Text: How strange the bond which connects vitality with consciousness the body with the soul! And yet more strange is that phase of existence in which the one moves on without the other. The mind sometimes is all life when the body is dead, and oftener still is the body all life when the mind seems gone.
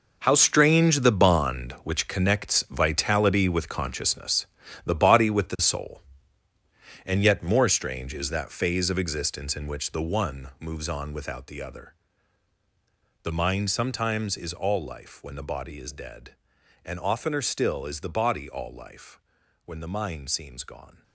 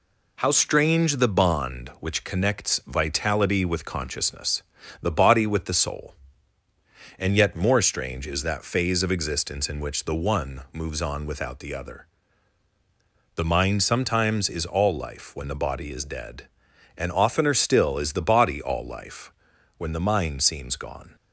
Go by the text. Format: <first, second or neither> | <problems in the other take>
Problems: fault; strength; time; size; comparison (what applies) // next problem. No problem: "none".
second | gets quieter; strong; throughout; 13 dB // pauses between "consciousness" and "the"; at 4.4 s; 0.38 s long; also in the second // pauses between "life" and "when"; noticeable; at 19.1 s; 0.46 s long; noticeable in the second